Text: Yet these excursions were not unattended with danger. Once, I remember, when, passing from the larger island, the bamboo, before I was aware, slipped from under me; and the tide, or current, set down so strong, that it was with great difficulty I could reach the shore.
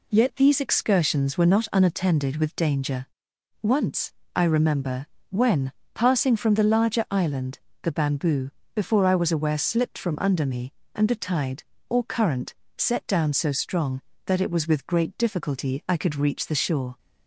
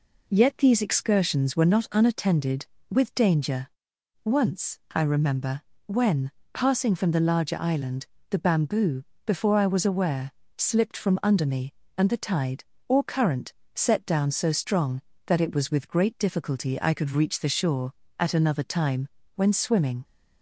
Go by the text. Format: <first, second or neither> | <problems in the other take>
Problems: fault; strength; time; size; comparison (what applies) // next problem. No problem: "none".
first | goes on to say "At another time when swimming"; strong; from 18.1 s on; 1.8 s long